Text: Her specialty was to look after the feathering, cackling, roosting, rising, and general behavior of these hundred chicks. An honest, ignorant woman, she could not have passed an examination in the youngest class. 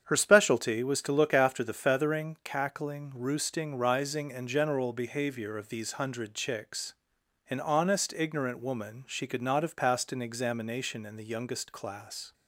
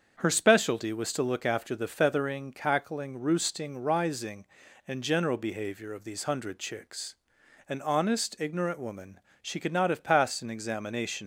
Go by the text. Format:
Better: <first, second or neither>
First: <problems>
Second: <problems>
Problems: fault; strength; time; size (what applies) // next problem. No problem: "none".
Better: first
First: starts louder than the rest; strong; until 1.0 s; 8 dB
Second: starts louder than the rest; until 1.2 s; 7 dB // stops before "in the youngest class"; at 11.2 s